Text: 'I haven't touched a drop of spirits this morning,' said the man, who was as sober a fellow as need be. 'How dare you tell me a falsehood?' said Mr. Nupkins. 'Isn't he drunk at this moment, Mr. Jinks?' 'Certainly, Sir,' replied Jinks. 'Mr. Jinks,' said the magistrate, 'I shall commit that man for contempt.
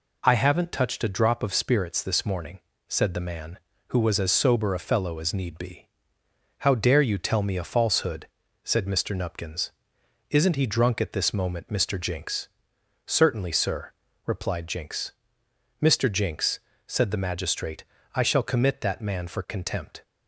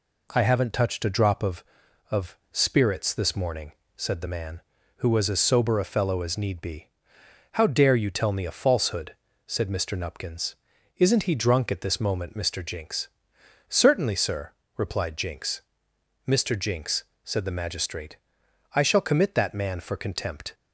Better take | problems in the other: first | says "of" twice; at 2.0 s

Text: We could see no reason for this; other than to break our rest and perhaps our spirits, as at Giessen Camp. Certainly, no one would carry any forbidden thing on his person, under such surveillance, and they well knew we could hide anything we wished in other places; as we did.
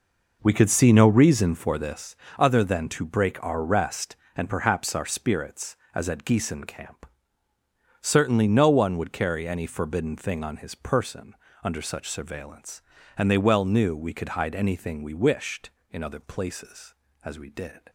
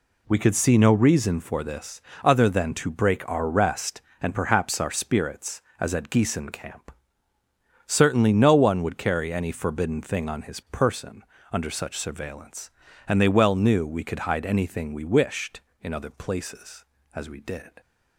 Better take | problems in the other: second | starts louder than the rest; noticeable; until 2.1 s; 5 dB

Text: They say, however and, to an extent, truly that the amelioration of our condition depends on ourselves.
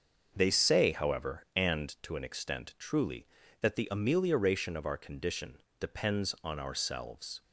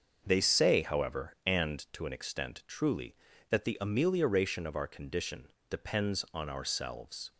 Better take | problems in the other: neither | starts louder than the rest; the same in both // pauses between "condition" and "depends"; slight; the same in both

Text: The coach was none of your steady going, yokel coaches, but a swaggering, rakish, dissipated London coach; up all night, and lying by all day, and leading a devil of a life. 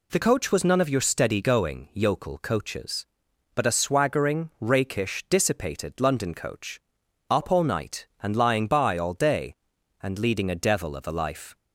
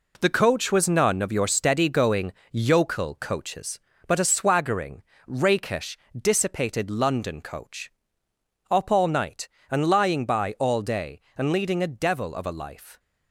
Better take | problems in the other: first | gets quieter; throughout; 7 dB

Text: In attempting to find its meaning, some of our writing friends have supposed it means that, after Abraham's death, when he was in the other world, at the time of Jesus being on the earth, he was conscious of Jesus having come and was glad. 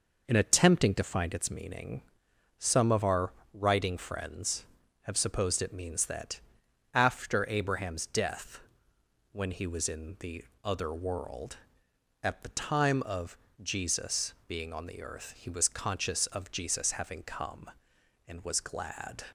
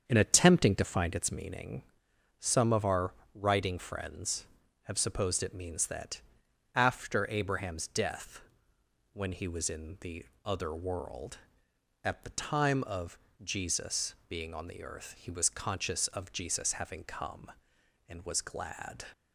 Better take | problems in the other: first | starts louder than the rest; strong; until 1.6 s; 7.5 dB // pauses between "our" and "writing"; slight; at 3.1 s; 0.22 s long; slight in the first // pauses between "the" and "other"; slight; at 10.2 s; 0.20 s long; slight in the first // pauses between "of" and "Jesus"; slight; at 13.1 s; 0.24 s long; slight in the first

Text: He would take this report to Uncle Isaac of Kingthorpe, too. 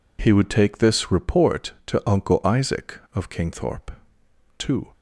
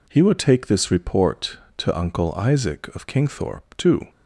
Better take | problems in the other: neither | none

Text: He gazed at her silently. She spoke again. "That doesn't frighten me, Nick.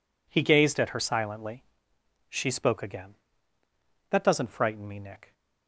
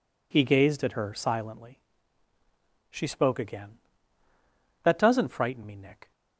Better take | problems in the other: neither | none

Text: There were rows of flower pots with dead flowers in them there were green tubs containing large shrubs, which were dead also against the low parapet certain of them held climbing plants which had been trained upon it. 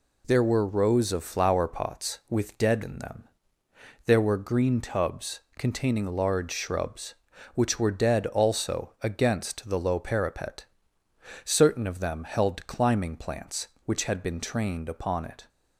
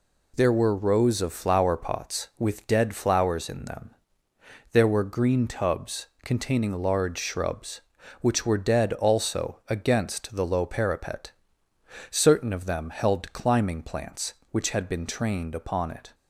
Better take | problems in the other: second | skips "flowers"; at 2.8 s // pauses between "them" and "there"; noticeable; at 3.2 s; 0.82 s long; noticeable in the second // pauses between "tubs" and "containing"; slight; at 5.4 s; 0.18 s long; slight in the second // pauses between "parapet" and "certain"; noticeable; at 10.6 s; 0.80 s long; noticeable in the second

